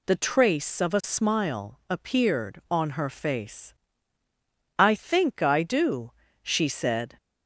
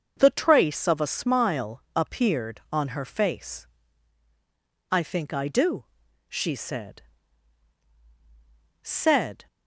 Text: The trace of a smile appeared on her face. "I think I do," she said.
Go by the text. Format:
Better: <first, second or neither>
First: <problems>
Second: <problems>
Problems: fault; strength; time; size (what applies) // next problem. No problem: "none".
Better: first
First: none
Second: starts louder than the rest; until 1.1 s; 6 dB // pauses between "smile" and "appeared"; slight; at 1.7 s; 0.16 s long // says "said" twice; at 8.8 s